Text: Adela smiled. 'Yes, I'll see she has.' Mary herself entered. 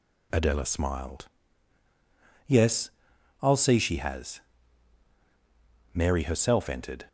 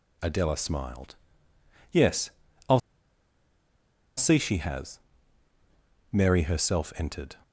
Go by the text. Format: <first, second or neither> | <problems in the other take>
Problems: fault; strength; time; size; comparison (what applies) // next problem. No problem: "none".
first | pauses between "I'll" and "see"; strong; at 2.8 s; 1.3 s long